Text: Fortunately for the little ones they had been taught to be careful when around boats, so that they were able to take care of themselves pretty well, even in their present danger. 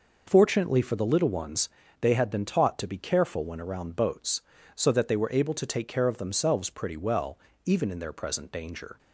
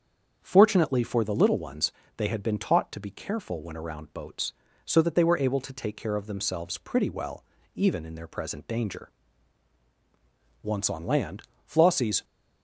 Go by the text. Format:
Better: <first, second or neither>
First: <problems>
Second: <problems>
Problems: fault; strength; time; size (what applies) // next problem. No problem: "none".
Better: first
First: pauses between "ones" and "they"; slight; at 1.6 s; 0.32 s long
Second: starts louder than the rest; strong; until 1.4 s; 7 dB // pauses between "ones" and "they"; slight; at 1.9 s; 0.24 s long // goes on to say "Once on land Flossie's"; from 10.6 s on; 1.6 s long